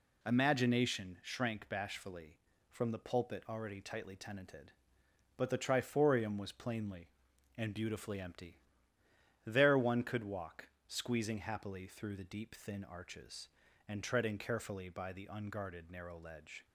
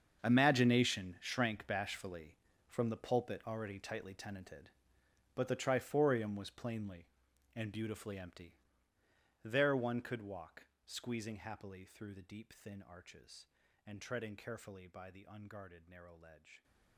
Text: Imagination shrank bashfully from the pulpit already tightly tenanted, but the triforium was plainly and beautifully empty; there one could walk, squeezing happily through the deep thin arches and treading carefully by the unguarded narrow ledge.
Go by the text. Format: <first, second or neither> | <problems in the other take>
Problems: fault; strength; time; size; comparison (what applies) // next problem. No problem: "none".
first | gets quieter; strong; throughout; 16.5 dB